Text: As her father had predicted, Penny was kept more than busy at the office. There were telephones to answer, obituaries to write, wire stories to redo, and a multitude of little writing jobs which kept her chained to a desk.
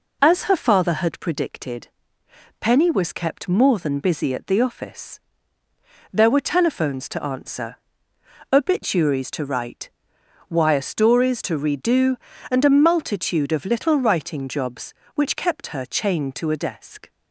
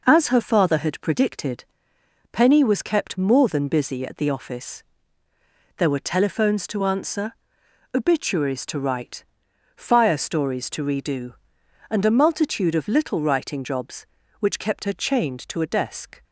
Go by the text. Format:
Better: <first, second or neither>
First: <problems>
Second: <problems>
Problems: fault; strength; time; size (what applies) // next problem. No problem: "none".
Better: first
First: none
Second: says "fire" for "wire"; at 9.7 s